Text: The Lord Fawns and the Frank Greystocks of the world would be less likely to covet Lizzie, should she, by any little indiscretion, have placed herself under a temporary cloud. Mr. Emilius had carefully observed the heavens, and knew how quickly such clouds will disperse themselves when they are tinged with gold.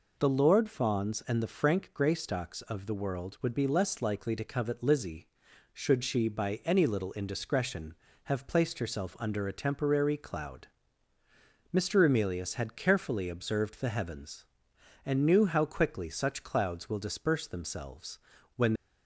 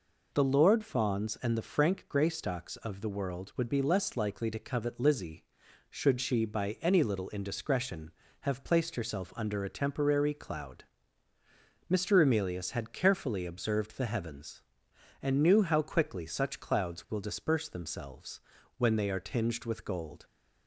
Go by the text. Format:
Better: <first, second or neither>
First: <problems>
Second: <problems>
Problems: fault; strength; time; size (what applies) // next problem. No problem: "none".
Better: second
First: pauses between "themselves" and "when"; slight; at 18.1 s; 0.36 s long // stops before "they are tinged with gold"; at 18.7 s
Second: pauses between "themselves" and "when"; slight; at 18.4 s; 0.36 s long